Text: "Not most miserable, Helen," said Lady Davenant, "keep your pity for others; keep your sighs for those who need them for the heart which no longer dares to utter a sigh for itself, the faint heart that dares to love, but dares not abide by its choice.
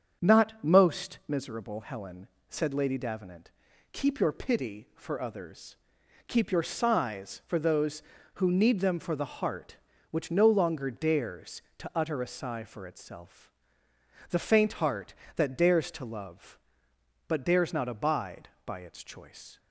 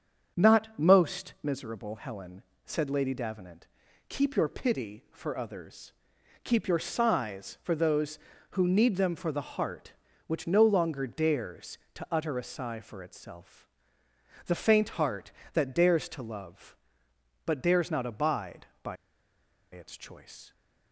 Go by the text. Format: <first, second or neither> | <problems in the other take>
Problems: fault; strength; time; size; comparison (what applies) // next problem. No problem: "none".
first | starts louder than the rest; strong; until 1.4 s; 7.5 dB; strong in the first // pauses between "by" and "its"; noticeable; at 18.9 s; 0.76 s long